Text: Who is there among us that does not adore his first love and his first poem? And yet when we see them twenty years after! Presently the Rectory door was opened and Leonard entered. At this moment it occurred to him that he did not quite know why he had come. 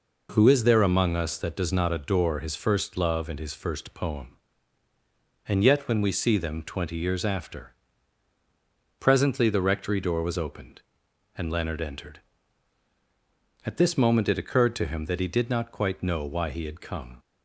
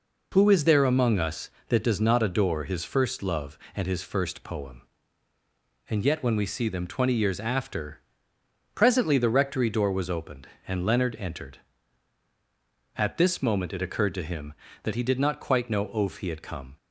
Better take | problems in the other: first | says "oaf" for "why"; at 15.8 s

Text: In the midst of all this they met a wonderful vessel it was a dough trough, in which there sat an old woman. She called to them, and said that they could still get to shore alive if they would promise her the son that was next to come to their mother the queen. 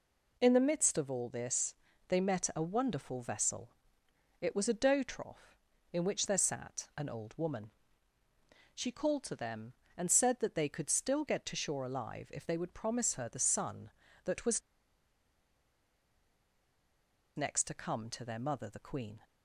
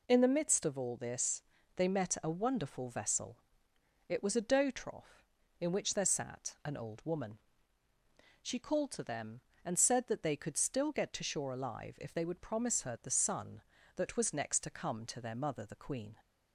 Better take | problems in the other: second | pauses between "this" and "they"; slight; at 1.7 s; 0.36 s long; slight in the second // pauses between "vessel" and "it"; noticeable; at 3.7 s; 0.68 s long; noticeable in the second // pauses between "was" and "next"; strong; at 14.6 s; 2.7 s long

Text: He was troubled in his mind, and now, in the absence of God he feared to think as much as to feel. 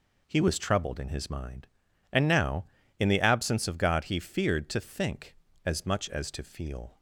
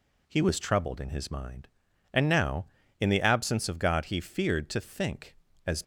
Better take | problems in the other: first | stops before "much as to feel"; at 5.8 s

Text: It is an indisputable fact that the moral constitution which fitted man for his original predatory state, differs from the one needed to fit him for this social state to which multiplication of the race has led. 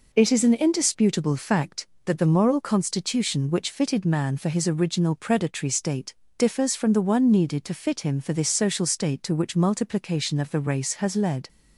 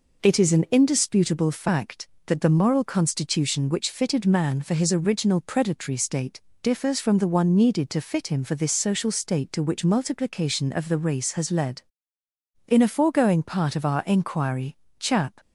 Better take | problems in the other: first | goes on to say "In a foregoing part of our inquiry Chap"; strong; from 12.6 s on; 2.7 s long

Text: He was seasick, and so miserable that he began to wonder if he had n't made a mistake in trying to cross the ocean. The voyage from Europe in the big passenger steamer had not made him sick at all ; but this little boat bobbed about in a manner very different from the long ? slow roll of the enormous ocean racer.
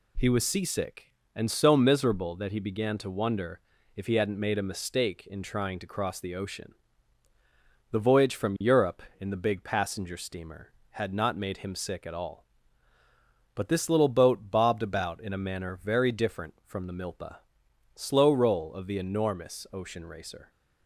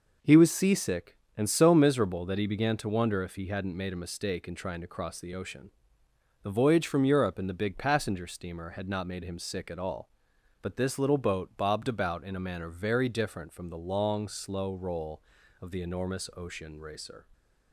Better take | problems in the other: second | pauses between "wonder" and "if"; slight; at 3.5 s; 0.36 s long // says "milpa" for "long"; at 16.9 s

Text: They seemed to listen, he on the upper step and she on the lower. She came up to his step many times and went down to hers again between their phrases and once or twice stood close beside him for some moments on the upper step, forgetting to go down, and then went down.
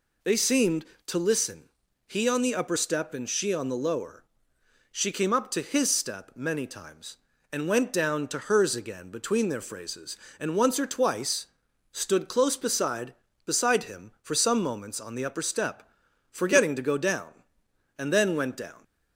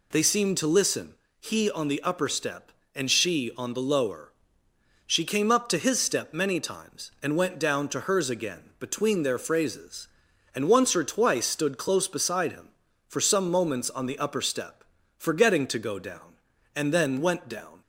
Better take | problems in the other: second | pauses between "twice" and "stood"; noticeable; at 11.4 s; 0.46 s long // says "beside" twice; at 13.4 s

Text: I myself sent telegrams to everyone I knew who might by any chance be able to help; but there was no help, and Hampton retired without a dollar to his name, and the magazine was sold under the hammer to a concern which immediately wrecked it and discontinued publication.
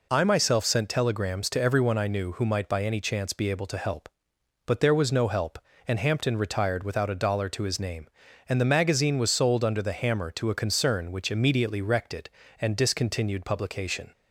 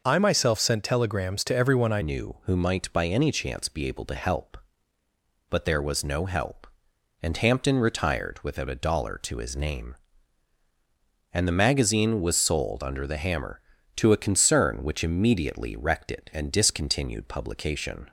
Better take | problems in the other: first | changes voice at "knew"; from 2.0 s on; 16.0 s long

